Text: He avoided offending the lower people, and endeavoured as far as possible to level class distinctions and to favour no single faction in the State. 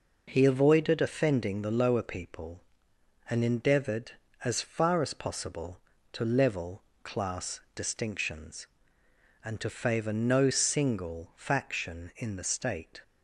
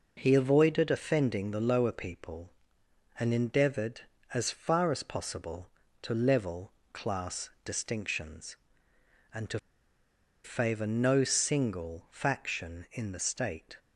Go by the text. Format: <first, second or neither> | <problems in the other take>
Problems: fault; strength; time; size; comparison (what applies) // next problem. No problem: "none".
first | pauses between "level" and "class"; slight; at 6.7 s; 0.20 s long; slight in the first // pauses between "to" and "favour"; noticeable; at 9.5 s; 0.84 s long